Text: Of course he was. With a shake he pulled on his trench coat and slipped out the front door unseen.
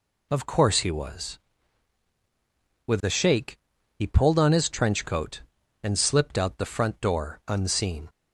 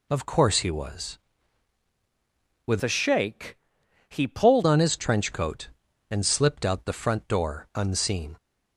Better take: first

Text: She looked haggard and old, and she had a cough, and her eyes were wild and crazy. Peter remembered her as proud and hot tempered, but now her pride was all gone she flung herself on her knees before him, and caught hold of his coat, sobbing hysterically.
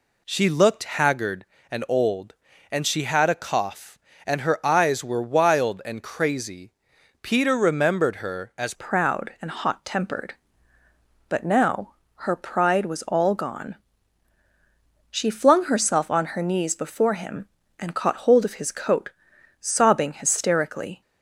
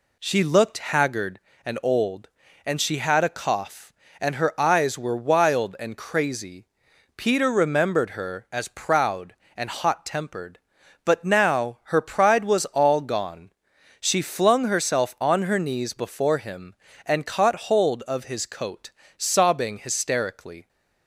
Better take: second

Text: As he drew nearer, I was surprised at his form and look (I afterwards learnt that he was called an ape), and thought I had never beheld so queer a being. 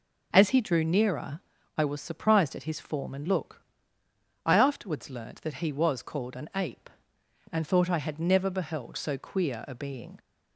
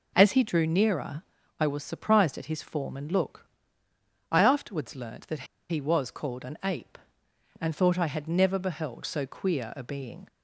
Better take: first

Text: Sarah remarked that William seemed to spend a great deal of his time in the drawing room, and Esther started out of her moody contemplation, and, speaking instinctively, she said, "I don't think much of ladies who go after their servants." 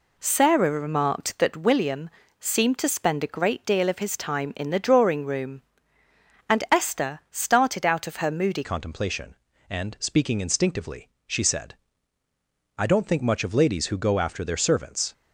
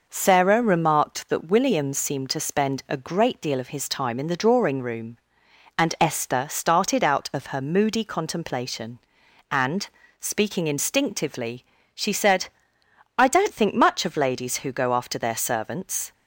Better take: second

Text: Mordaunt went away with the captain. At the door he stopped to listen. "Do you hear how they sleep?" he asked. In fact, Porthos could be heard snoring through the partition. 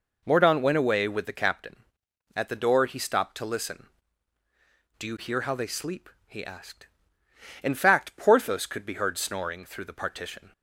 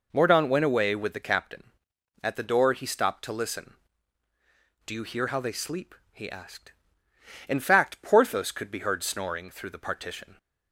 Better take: neither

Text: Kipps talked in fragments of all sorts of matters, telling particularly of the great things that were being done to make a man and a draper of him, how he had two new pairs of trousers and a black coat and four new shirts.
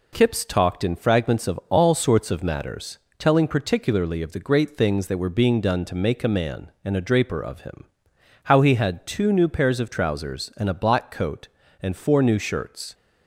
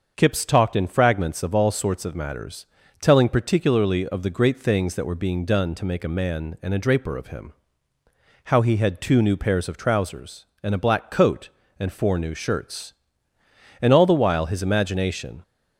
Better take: first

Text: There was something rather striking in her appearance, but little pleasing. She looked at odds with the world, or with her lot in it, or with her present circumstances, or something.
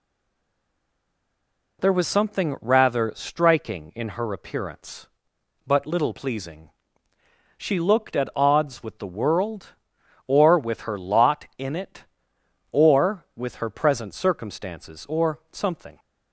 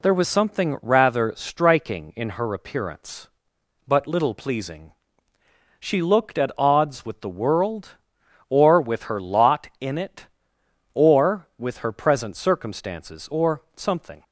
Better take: second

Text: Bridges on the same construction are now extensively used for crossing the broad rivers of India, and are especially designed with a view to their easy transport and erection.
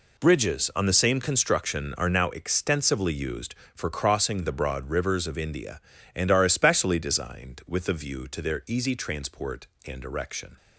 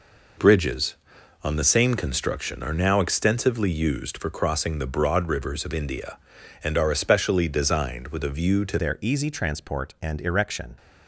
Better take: first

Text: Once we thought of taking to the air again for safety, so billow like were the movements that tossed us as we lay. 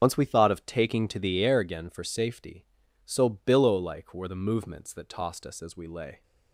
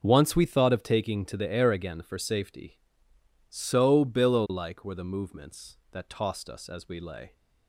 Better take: second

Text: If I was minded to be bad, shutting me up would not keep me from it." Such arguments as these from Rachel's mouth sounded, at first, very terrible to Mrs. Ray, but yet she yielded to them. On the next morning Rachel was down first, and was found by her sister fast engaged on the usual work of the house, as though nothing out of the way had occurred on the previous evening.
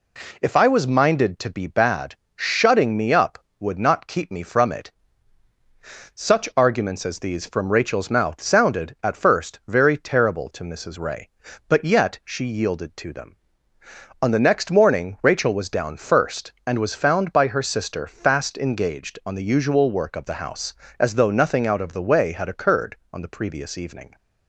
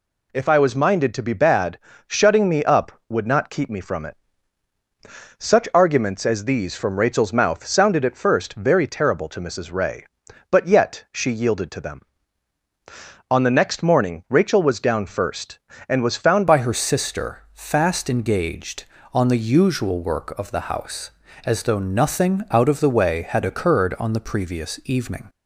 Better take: first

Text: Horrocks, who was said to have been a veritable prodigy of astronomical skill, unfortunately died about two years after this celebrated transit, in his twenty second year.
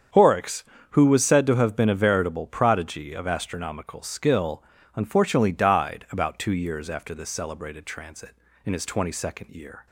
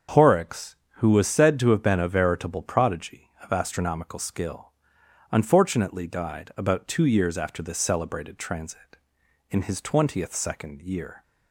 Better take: first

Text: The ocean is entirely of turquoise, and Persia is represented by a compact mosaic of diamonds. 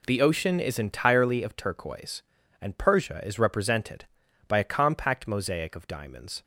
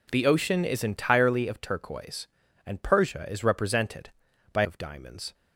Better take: first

